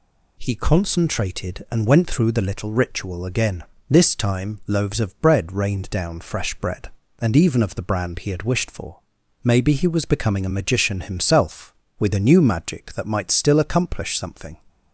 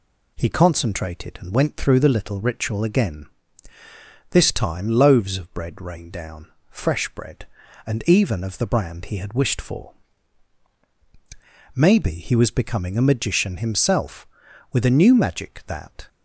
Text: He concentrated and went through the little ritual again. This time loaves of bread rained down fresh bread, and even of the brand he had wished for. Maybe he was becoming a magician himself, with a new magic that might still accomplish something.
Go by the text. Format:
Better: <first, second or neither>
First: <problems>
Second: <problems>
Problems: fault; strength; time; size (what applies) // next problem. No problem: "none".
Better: first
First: none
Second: pauses between "down" and "fresh"; slight; at 6.4 s; 0.20 s long // stops before "might still accomplish something"; at 16.0 s